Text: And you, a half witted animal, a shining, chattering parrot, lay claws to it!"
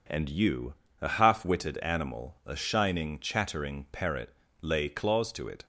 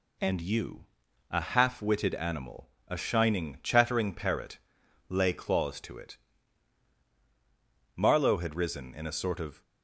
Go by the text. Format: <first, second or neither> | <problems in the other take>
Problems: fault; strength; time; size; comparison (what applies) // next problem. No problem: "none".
first | goes on to say "Marlowe had risen in a sort of"; from 7.9 s on; 1.6 s long